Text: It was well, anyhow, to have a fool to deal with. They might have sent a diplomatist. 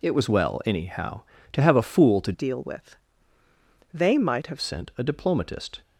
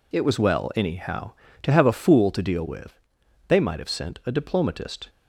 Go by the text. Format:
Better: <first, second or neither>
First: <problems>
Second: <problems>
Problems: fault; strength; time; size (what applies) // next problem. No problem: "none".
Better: second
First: changes voice from "deal" to "have"; from 2.3 to 4.5 s; 2.2 s long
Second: none